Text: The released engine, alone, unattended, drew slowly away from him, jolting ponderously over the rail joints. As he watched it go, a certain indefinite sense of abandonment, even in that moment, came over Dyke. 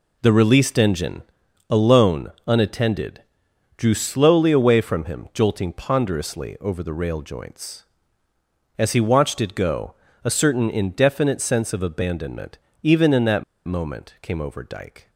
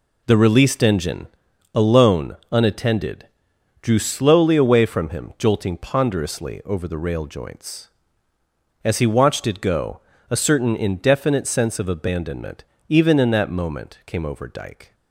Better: second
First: pauses between "that" and "moment"; slight; at 13.4 s; 0.22 s long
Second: none

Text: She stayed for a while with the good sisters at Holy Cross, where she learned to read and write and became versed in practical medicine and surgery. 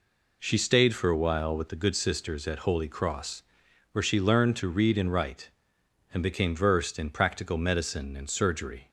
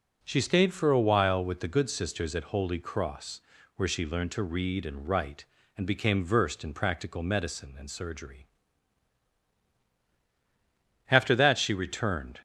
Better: first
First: none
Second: goes on to say "After that she returned"; from 11.0 s on; 1.3 s long

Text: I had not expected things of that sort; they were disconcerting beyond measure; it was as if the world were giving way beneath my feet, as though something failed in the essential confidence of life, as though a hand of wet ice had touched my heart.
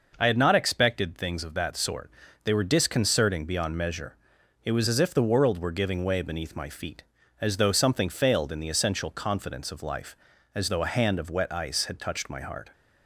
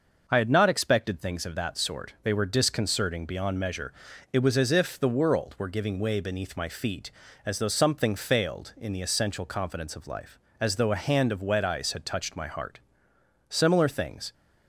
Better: first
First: none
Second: starts louder than the rest; noticeable; until 1.2 s; 6 dB // goes on to say "Similar things"; noticeable; from 13.4 s on; 0.86 s long

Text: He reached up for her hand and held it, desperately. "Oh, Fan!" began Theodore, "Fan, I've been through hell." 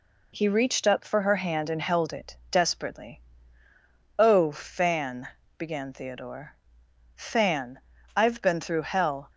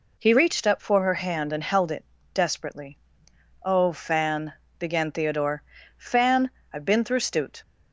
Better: first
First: none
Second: says "stute" for "hell"; at 7.1 s

